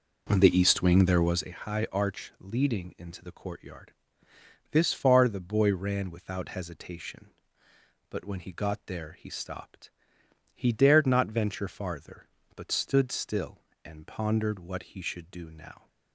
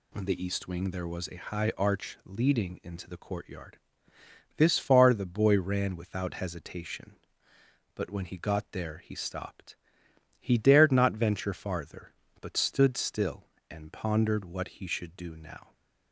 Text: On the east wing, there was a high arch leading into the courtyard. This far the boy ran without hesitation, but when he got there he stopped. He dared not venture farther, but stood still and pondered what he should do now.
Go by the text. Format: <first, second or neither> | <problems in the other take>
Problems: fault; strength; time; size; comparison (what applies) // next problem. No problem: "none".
second | starts louder than the rest; noticeable; until 1.6 s; 5 dB